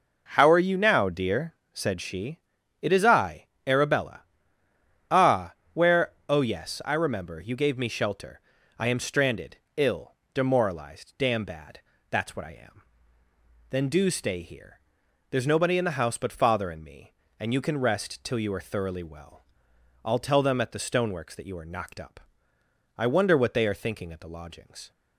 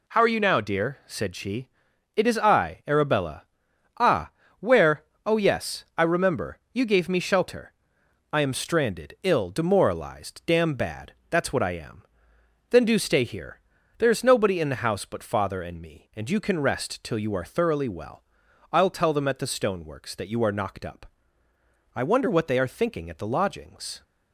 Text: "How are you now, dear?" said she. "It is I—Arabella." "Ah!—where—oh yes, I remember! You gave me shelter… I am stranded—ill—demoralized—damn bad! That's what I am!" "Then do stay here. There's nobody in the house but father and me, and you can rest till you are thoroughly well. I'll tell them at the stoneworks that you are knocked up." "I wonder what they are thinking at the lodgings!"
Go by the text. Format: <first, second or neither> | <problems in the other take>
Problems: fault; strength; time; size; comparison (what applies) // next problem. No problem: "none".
neither | none